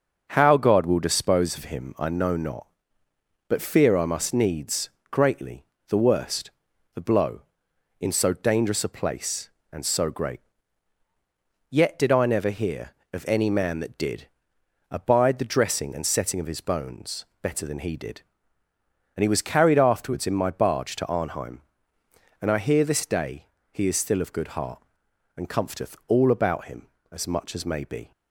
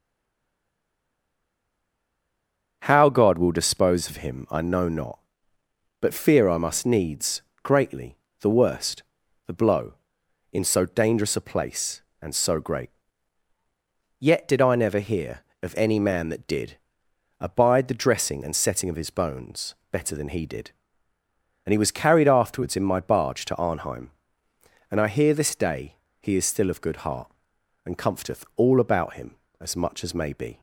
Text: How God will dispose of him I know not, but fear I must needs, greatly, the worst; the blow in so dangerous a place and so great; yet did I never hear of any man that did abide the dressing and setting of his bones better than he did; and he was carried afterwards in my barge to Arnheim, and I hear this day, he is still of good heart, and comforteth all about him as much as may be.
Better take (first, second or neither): first